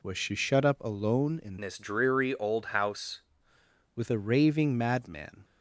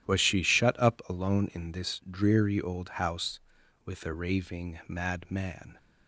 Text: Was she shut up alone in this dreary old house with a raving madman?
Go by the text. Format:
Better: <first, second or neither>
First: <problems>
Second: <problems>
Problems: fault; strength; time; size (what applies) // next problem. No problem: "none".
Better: second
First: changes voice from "this" to "house"; from 1.6 to 3.2 s; 1.6 s long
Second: none